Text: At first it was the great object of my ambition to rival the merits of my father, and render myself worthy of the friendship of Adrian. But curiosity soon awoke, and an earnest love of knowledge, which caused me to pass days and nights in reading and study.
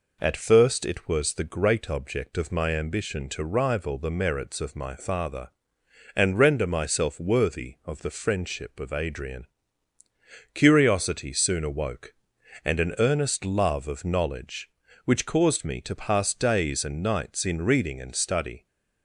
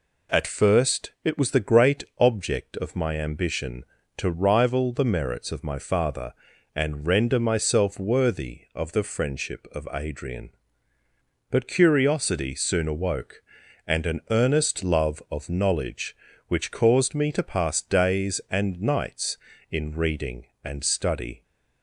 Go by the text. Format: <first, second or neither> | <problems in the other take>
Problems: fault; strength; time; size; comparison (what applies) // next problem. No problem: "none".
second | skips "But"; at 10.0 s